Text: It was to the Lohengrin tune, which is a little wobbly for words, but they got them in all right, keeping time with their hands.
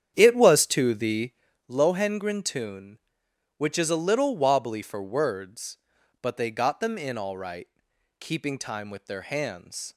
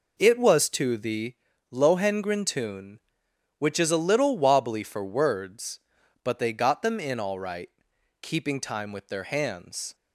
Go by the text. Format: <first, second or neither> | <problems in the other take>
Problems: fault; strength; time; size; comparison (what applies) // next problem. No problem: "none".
second | starts louder than the rest; strong; until 1.7 s; 9 dB // pauses between "the" and "Lohengrin"; at 1.3 s; 0.38 s long; also in the second